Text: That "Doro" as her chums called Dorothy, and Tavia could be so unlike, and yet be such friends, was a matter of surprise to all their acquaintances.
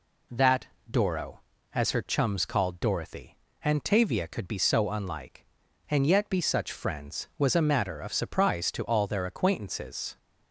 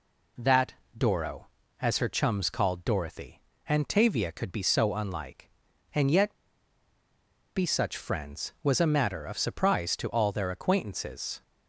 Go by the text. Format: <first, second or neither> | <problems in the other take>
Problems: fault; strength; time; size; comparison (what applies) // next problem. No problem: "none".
first | pauses between "That" and "Doro"; slight; at 0.7 s; 0.24 s long; slight in the first // pauses between "yet" and "be"; at 6.3 s; 1.2 s long